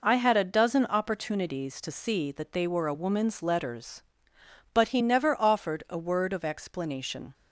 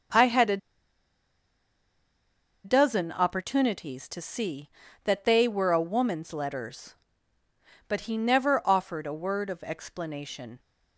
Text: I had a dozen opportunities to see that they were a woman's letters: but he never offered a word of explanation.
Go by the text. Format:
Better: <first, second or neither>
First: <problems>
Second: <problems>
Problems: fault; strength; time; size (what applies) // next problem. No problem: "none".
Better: first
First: none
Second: starts louder than the rest; until 3.2 s; 6 dB // pauses between "a" and "dozen"; strong; at 0.5 s; 2.0 s long